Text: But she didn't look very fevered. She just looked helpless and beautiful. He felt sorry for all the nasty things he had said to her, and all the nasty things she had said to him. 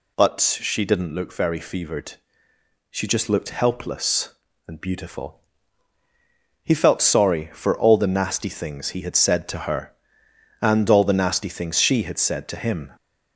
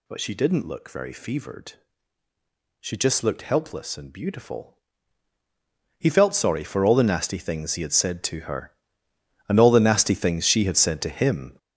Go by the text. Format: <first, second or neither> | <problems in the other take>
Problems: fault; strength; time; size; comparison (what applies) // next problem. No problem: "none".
first | gets louder; strong; throughout; 8 dB